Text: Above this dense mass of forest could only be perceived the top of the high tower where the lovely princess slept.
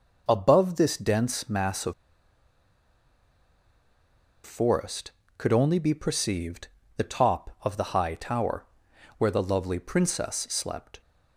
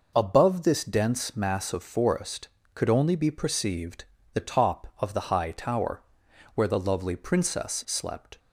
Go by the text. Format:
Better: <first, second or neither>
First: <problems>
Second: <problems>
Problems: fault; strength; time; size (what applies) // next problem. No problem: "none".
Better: second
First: pauses between "of" and "forest"; strong; at 1.9 s; 2.5 s long // pauses between "perceived" and "the"; slight; at 6.6 s; 0.30 s long // pauses between "tower" and "where"; noticeable; at 8.6 s; 0.52 s long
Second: pauses between "perceived" and "the"; slight; at 4.0 s; 0.30 s long // pauses between "tower" and "where"; noticeable; at 6.0 s; 0.52 s long